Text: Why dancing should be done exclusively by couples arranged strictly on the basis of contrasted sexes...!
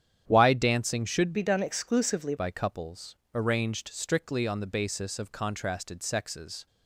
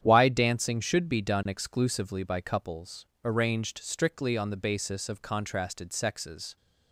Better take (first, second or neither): second